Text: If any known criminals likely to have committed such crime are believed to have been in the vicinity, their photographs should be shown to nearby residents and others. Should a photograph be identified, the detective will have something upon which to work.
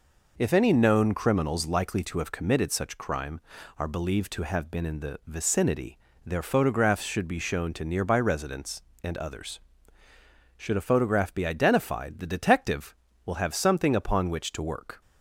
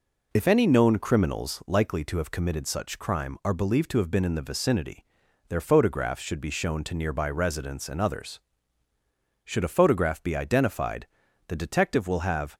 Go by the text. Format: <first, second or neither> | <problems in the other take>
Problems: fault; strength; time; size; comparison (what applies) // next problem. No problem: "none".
first | stops before "something upon which to work"; at 12.5 s